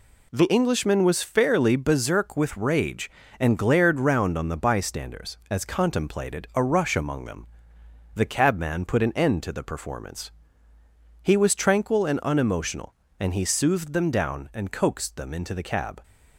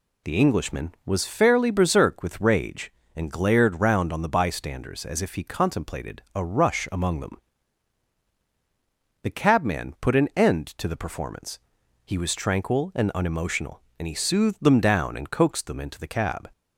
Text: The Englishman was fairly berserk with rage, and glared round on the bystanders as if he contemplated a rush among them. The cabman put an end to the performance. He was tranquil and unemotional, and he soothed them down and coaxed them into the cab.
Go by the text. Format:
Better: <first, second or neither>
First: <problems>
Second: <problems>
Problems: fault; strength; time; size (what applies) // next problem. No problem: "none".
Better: second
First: skips "if he"; at 5.6 s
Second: none